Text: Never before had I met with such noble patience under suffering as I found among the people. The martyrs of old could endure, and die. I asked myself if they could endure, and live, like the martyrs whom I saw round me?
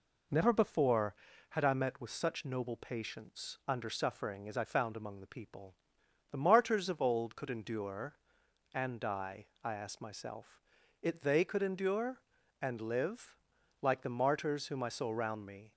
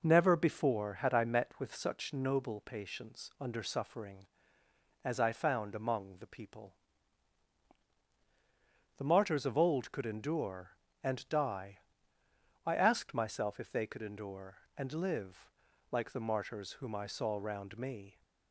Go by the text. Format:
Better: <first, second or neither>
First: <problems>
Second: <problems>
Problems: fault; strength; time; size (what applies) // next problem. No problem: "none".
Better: second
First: says "it" for "if"; at 11.0 s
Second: none